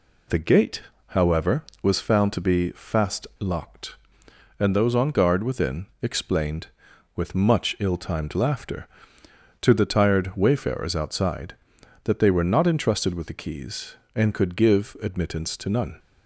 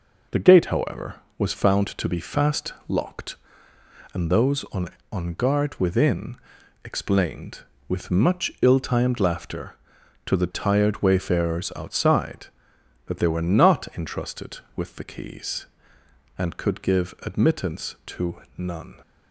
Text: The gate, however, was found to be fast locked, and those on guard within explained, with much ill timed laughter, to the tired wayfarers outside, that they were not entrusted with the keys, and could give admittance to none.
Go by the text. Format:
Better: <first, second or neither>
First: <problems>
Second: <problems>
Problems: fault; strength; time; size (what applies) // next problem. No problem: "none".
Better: first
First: pauses between "fast" and "locked"; slight; at 3.2 s; 0.15 s long // pauses between "within" and "explained"; slight; at 5.8 s; 0.16 s long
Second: pauses between "fast" and "locked"; slight; at 2.7 s; 0.16 s long // says "on" twice; at 5.1 s // pauses between "within" and "explained"; noticeable; at 6.3 s; 0.46 s long // pauses between "to" and "none"; slight; at 18.3 s; 0.16 s long